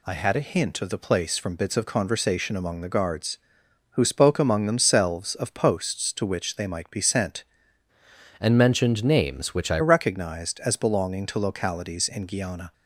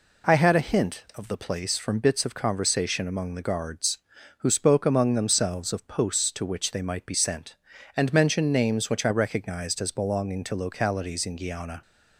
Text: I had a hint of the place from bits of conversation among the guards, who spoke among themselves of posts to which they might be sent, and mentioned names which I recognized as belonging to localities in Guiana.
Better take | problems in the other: second | changes voice from "and" to "I"; from 8.3 to 9.7 s; 1.4 s long

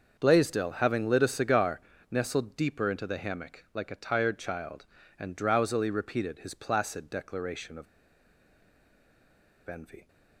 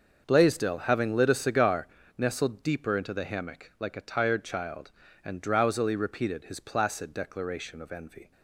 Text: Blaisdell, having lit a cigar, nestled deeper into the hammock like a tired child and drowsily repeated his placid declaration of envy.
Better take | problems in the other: second | starts louder than the rest; until 1.2 s; 6.5 dB; also in the second // pauses between "of" and "envy"; strong; at 7.8 s; 1.8 s long

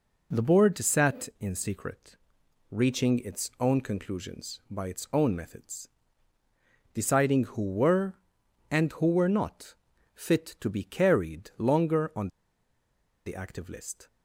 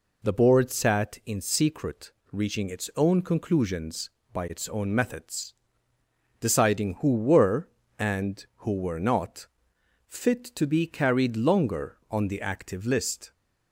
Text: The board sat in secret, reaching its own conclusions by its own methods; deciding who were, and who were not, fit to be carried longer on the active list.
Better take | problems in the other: second | pauses between "on" and "the"; noticeable; at 12.2 s; 0.96 s long

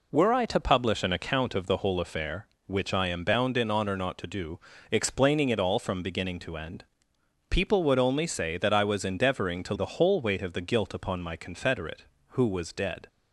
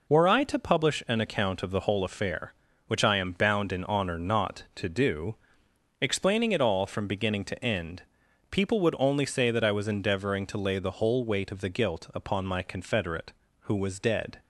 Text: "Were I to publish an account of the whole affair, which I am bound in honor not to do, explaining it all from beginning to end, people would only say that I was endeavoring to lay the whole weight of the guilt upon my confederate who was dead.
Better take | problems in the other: second | skips "lay"; at 9.7 s

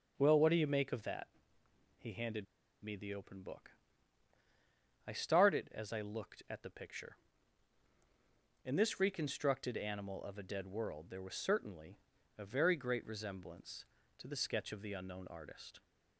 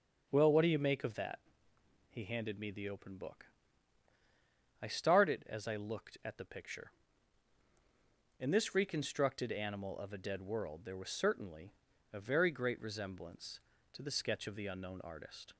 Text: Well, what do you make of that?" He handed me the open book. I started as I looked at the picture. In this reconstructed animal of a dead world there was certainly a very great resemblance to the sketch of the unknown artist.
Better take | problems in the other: second | starts louder than the rest; until 1.1 s; 7 dB; also in the second // pauses between "handed" and "me"; at 2.4 s; 0.38 s long // pauses between "certainly" and "a"; at 11.9 s; 0.40 s long; also in the second

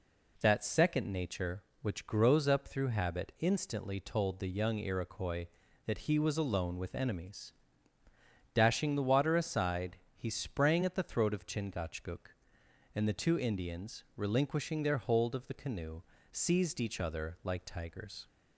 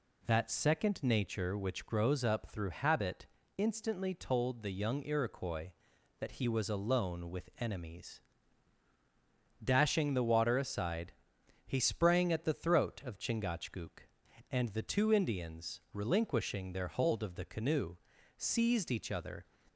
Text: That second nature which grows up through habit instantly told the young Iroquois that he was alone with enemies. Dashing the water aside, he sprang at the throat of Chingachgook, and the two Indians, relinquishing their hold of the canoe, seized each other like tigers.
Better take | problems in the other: first | pauses between "habit" and "instantly"; slight; at 3.2 s; 0.32 s long // stops before "like tigers"; at 19.6 s

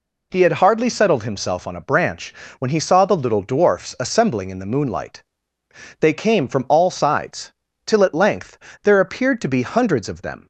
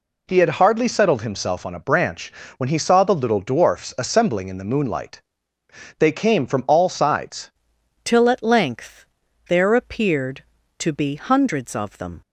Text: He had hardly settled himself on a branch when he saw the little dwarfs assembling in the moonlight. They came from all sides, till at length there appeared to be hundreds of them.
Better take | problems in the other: first | pauses between "branch" and "when"; slight; at 2.3 s; 0.24 s long; slight in the first // changes voice at "till"; from 8.0 s on; 4.2 s long // pauses between "length" and "there"; noticeable; at 9.0 s; 0.46 s long; slight in the first

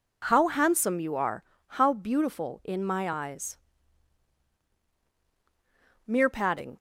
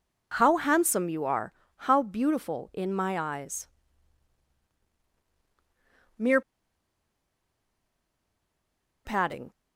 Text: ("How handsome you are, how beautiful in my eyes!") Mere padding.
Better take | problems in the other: first | pauses between "Mere" and "padding"; strong; at 6.4 s; 2.6 s long

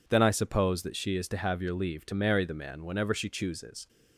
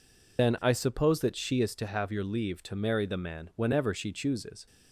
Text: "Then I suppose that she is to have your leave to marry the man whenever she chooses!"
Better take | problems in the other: first | loses the start of "Then"; at 0.3 s; 85 ms

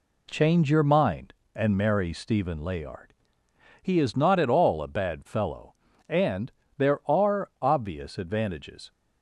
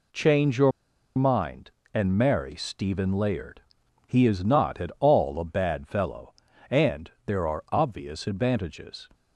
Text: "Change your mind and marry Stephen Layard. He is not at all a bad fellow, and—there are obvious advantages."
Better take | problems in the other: first | pauses between "your" and "mind"; at 0.7 s; 0.45 s long

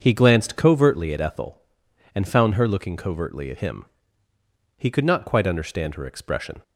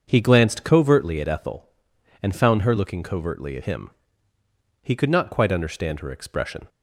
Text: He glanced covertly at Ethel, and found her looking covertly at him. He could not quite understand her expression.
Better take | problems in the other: neither | starts louder than the rest; the same in both

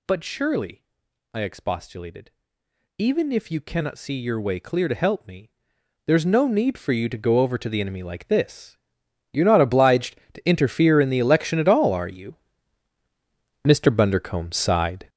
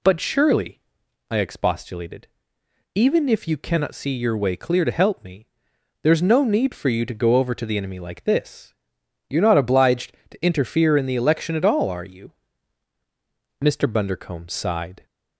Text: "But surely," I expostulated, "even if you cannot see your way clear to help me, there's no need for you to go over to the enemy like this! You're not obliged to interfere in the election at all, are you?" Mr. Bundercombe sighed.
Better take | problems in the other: second | gets louder; strong; throughout; 10 dB

